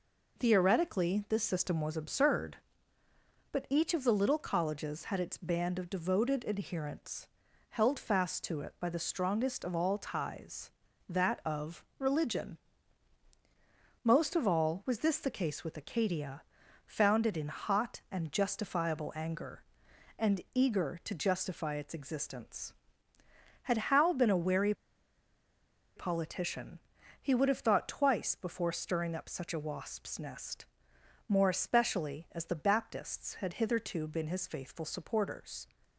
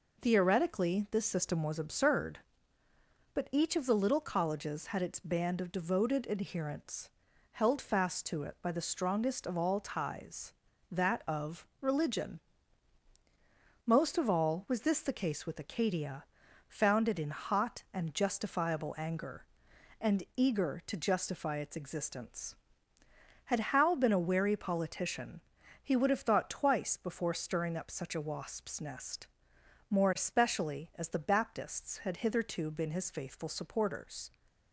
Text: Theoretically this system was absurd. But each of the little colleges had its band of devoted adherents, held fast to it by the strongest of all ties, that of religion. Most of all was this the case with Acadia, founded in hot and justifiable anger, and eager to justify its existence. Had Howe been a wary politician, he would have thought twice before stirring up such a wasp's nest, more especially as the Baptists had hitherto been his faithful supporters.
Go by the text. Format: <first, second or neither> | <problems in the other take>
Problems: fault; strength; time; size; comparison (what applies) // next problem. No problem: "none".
second | pauses between "of" and "religion"; slight; at 11.8 s; 0.16 s long; slight in the second // pauses between "wary" and "politician"; at 24.7 s; 1.2 s long